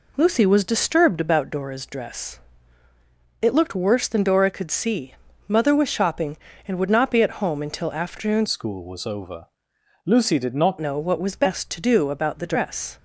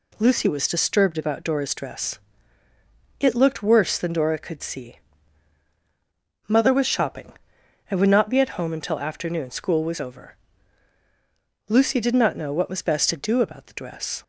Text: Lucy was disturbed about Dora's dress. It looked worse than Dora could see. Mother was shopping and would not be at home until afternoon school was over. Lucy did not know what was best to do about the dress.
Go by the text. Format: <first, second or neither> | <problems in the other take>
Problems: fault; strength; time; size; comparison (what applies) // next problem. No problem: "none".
second | changes voice from "school" to "not"; from 8.4 to 10.7 s; 2.3 s long